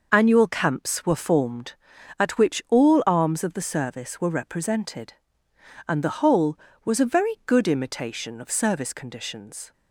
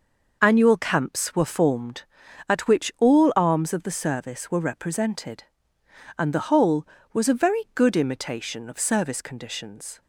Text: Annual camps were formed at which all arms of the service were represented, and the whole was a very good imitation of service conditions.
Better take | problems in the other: neither | none

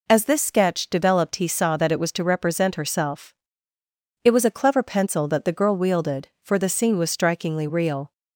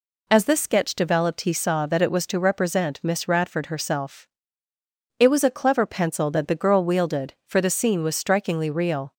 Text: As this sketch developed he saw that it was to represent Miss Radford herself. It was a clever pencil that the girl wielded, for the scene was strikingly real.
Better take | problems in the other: second | skips "Miss Radford"; at 2.7 s

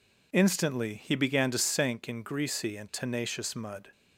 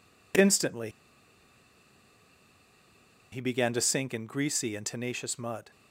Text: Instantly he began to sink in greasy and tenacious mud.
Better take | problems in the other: first | pauses between "Instantly" and "he"; strong; at 0.8 s; 2.4 s long

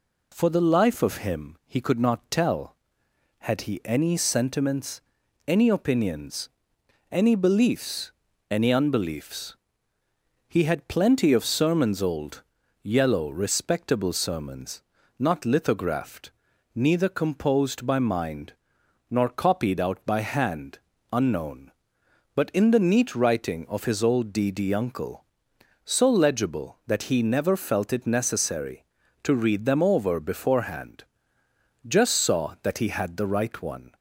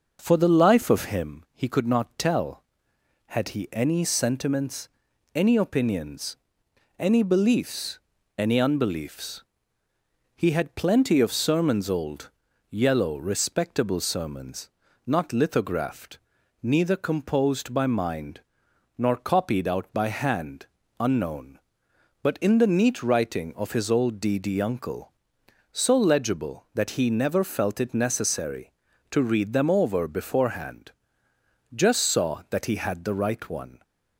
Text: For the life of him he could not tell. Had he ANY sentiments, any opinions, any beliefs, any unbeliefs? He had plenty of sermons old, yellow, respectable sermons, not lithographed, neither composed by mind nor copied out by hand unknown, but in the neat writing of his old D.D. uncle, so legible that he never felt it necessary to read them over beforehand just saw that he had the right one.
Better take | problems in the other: first | starts louder than the rest; noticeable; until 1.3 s; 6 dB // pauses between "mind" and "nor"; noticeable; at 18.4 s; 0.58 s long; noticeable in the first // pauses between "hand" and "unknown"; slight; at 20.6 s; 0.34 s long; slight in the first // pauses between "beforehand" and "just"; noticeable; at 30.9 s; 0.82 s long; noticeable in the first

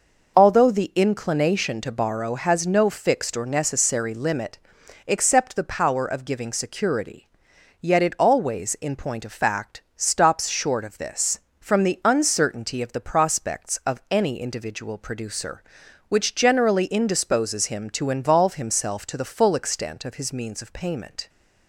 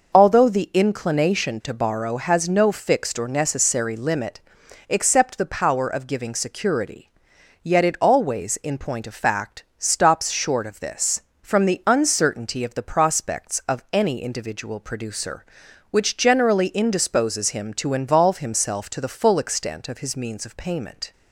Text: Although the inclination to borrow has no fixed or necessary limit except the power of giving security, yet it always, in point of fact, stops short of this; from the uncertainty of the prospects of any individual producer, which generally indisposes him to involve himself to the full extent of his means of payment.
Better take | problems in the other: neither | pauses between "limit" and "except"; noticeable; the same in both

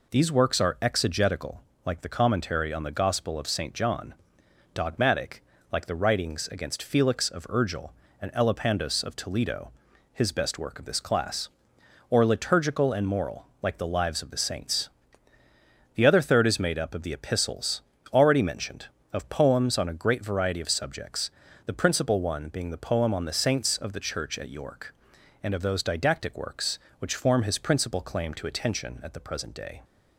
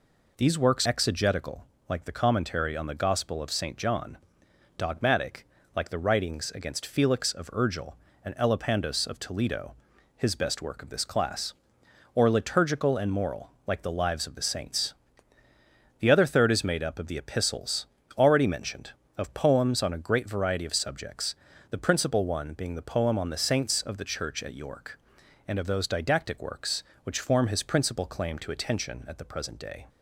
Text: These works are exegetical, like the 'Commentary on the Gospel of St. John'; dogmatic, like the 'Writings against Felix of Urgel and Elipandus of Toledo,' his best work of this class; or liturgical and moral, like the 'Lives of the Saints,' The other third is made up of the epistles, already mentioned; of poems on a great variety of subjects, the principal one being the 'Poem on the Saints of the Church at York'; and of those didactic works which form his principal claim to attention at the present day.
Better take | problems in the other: first | skips "are"; at 0.8 s

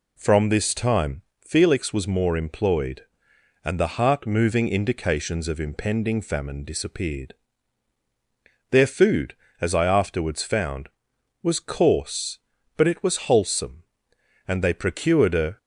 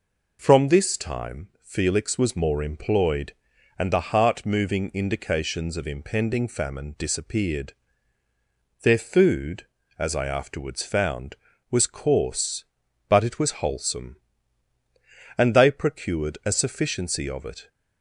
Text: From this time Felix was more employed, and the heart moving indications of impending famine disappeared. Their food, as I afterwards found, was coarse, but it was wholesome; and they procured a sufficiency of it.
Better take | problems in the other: second | pauses between "time" and "Felix"; slight; at 1.2 s; 0.20 s long // stops before "sufficiency of it"; at 15.5 s

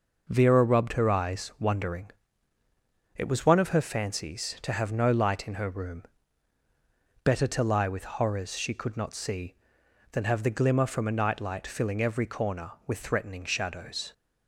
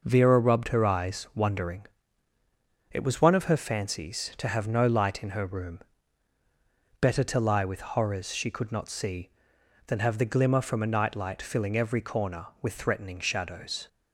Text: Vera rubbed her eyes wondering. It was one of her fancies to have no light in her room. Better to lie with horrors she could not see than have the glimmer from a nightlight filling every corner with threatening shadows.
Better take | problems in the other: neither | none

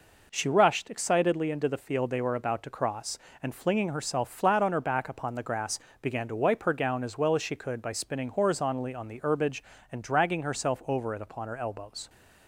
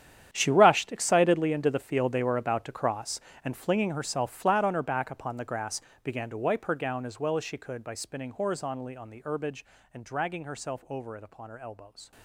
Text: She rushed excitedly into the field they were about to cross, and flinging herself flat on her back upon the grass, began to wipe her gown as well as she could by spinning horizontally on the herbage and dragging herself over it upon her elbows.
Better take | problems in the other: first | gets quieter; strong; throughout; 16.5 dB

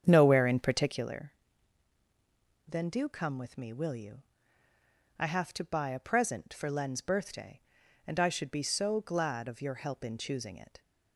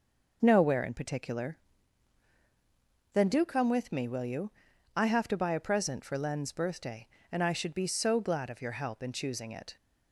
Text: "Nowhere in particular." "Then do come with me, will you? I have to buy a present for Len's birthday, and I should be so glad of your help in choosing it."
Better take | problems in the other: second | starts louder than the rest; strong; until 1.2 s; 8.5 dB

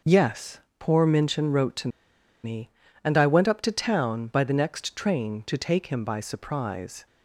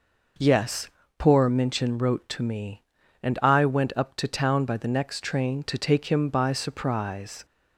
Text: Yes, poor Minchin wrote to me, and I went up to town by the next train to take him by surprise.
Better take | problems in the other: second | pauses between "to" and "me"; noticeable; at 1.8 s; 0.55 s long

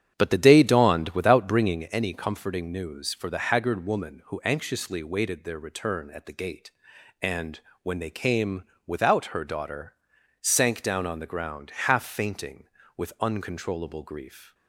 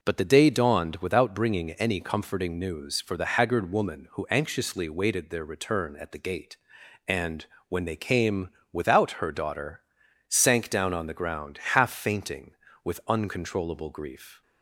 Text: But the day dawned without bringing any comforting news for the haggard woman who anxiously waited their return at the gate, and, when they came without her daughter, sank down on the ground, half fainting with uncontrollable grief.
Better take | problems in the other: second | starts louder than the rest; strong; until 1.9 s; 8.5 dB // pauses between "came" and "without"; slight; at 8.6 s; 0.22 s long; slight in the second

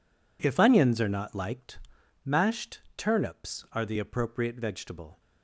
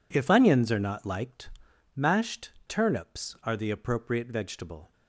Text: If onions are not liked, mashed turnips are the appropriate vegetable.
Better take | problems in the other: neither | pauses between "mashed" and "turnips"; slight; the same in both

